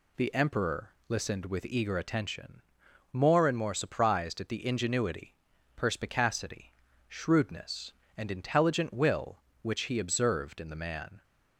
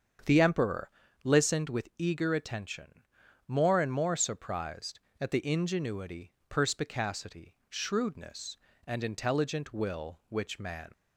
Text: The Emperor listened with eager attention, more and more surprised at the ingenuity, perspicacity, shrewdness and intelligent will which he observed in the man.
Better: first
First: pauses between "Emperor" and "listened"; slight; at 0.9 s; 0.18 s long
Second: starts louder than the rest; strong; until 1.5 s; 7.5 dB // pauses between "Emperor" and "listened"; slight; at 0.9 s; 0.34 s long // skips "he observed in the"; at 10.5 s

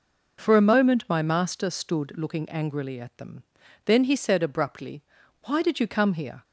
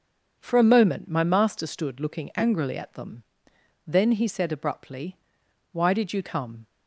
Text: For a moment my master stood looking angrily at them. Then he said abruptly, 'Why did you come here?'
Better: first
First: none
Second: starts louder than the rest; until 1.3 s; 6.5 dB // stops before "here"; at 6.6 s

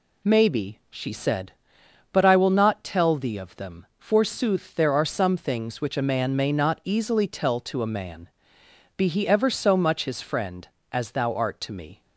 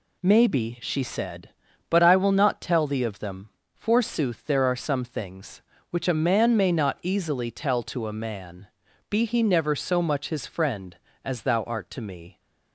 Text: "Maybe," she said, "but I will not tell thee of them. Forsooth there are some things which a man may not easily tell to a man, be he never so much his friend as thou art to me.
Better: second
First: says "ever" for "never"; at 9.2 s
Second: none

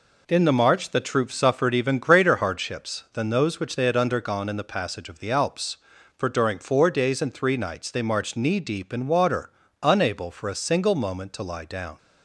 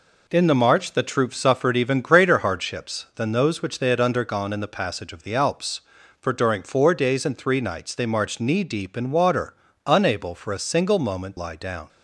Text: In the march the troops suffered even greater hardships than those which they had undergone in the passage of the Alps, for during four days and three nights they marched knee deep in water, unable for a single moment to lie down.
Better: first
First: none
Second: skips "to"; at 11.3 s

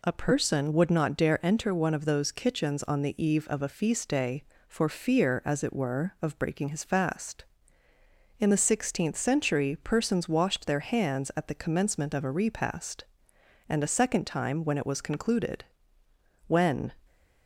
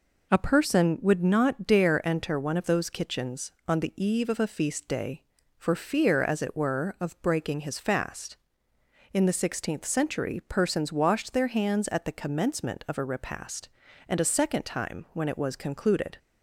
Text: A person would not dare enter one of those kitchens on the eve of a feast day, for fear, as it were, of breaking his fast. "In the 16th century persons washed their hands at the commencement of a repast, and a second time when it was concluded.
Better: second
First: goes on to say "When"; slight; from 16.4 s on; 0.46 s long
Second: none

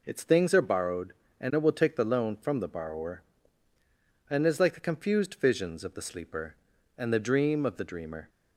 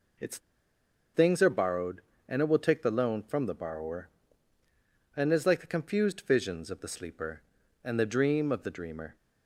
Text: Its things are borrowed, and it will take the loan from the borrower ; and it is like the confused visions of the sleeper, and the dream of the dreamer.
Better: first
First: none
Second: pauses between "Its" and "things"; noticeable; at 0.3 s; 0.76 s long

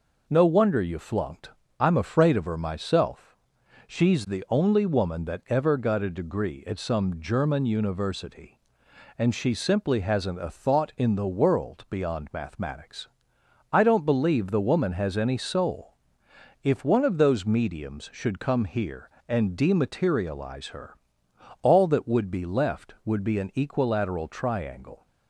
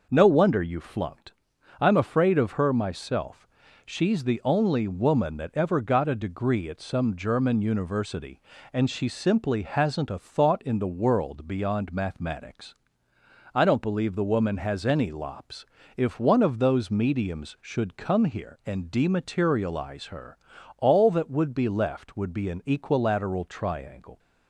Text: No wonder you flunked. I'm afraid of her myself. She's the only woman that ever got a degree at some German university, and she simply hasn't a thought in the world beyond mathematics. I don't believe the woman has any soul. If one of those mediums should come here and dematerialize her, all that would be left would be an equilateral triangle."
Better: first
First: none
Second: says "lops" for "soul"; at 15.0 s

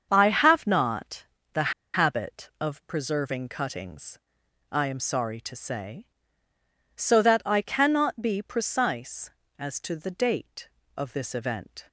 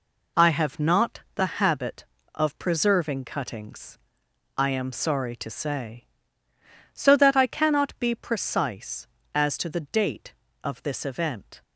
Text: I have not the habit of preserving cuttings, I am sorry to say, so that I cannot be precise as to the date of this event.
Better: second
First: starts louder than the rest; until 1.1 s; 7 dB // pauses between "not" and "the"; slight; at 1.2 s; 0.28 s long // pauses between "the" and "habit"; slight; at 1.7 s; 0.22 s long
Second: none

